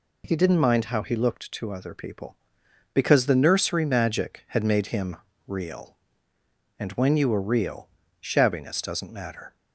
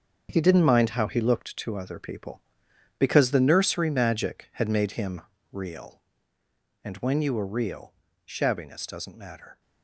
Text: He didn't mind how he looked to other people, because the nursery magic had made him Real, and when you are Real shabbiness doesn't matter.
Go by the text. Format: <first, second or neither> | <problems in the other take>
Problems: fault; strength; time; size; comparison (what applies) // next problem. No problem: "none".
first | gets quieter; strong; throughout; 10 dB // pauses between "him" and "Real"; slight; at 5.2 s; 0.30 s long; slight in the first // pauses between "Real" and "shabbiness"; slight; at 7.9 s; 0.30 s long; slight in the first